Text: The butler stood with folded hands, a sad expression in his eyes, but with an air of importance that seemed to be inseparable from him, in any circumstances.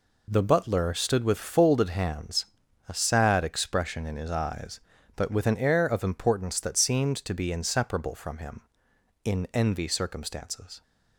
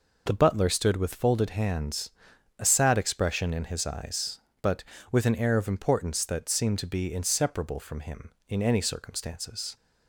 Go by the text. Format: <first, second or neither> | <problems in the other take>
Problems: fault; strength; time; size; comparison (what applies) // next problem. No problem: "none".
second | says "envy" for "any"; at 9.5 s